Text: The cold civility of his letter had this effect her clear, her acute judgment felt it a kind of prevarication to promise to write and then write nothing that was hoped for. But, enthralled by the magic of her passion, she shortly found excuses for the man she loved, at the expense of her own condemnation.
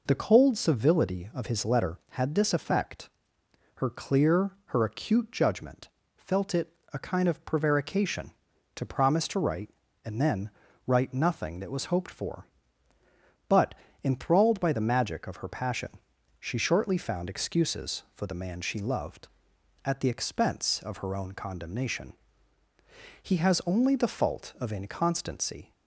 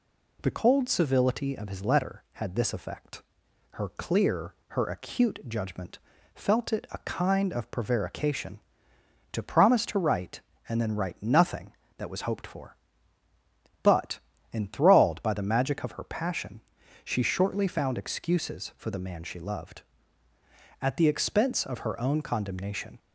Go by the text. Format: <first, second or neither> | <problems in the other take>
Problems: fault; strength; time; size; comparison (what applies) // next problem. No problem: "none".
second | pauses between "effect" and "her"; noticeable; at 3.0 s; 0.68 s long; noticeable in the second // pauses between "judgment" and "felt"; slight; at 5.8 s; 0.28 s long; slight in the second // pauses between "it" and "a"; slight; at 6.7 s; 0.24 s long // pauses between "then" and "write"; at 10.4 s; 0.38 s long // goes on to say "He has only the fault of inconstancy"; strong; from 23.2 s on; 2.5 s long